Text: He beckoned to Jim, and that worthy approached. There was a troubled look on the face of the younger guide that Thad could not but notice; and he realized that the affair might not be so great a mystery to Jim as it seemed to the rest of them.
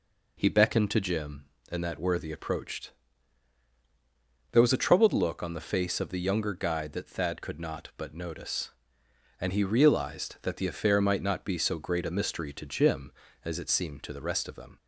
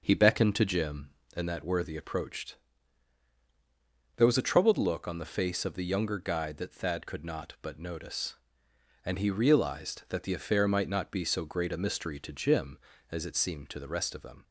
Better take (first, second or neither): first